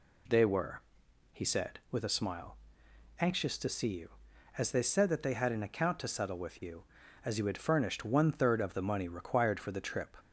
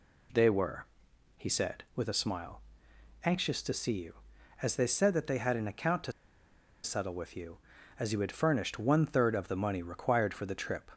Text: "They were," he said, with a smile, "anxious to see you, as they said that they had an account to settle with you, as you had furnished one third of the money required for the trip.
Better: first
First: none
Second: pauses between "to" and "settle"; noticeable; at 6.1 s; 0.72 s long

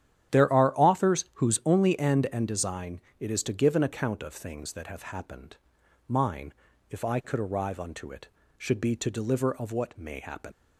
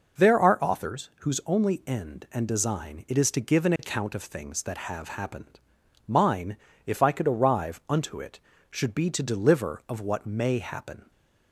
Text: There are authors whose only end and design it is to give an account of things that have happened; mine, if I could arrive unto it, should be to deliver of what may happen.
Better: second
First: starts louder than the rest; strong; until 1.4 s; 10.5 dB // pauses between "design" and "it"; slight; at 3.0 s; 0.18 s long // leaves "happen" unfinished; at 10.5 s; 105 ms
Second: none

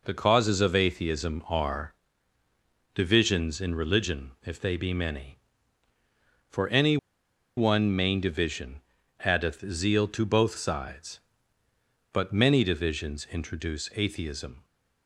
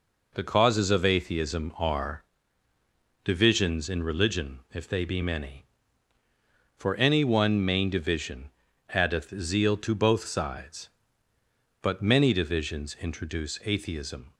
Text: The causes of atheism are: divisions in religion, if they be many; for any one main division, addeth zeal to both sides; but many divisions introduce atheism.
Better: second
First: pauses between "any" and "one"; noticeable; at 6.9 s; 0.60 s long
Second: none

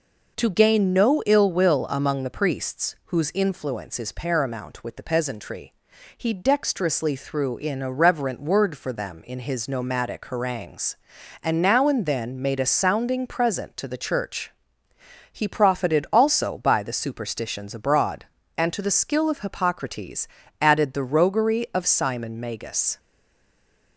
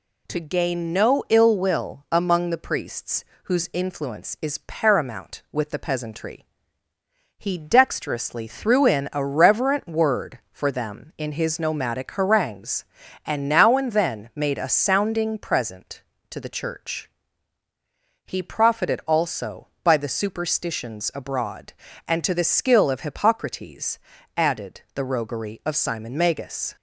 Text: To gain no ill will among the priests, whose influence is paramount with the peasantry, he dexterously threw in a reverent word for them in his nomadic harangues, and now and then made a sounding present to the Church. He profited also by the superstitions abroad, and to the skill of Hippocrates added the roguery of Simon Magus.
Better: second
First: pauses between "Hippocrates" and "added"; slight; at 20.2 s; 0.34 s long // stays silent after the last word; from 22.9 s on; 1.0 s long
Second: pauses between "Hippocrates" and "added"; slight; at 23.9 s; 0.36 s long

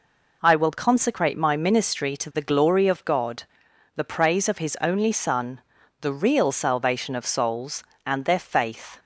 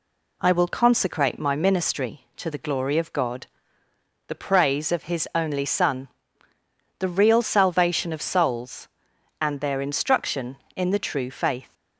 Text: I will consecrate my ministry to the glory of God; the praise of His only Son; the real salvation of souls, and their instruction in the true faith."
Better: second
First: skips "instruction in the true"; at 8.3 s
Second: none

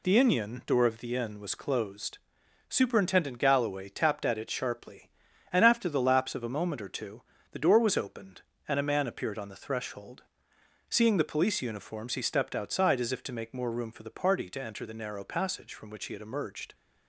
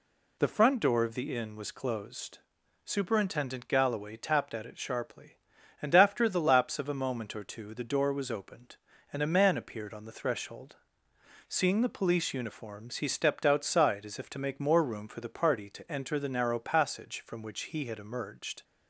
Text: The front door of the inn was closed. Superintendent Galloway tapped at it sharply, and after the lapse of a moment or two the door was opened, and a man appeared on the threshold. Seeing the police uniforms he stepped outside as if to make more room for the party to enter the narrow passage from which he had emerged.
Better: second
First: says "inion" for "front"; at 0.1 s // pauses between "two" and "the"; slight; at 7.2 s; 0.30 s long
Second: none

